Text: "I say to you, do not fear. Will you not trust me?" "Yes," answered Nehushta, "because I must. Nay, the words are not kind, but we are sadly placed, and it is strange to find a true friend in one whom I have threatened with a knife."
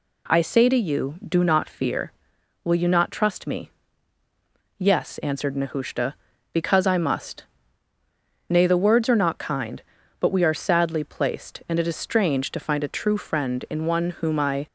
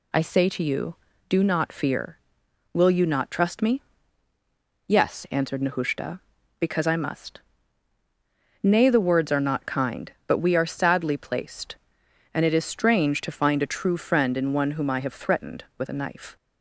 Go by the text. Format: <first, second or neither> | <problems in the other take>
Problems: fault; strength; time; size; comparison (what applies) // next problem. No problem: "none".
second | stops before "have threatened with a knife"; at 14.6 s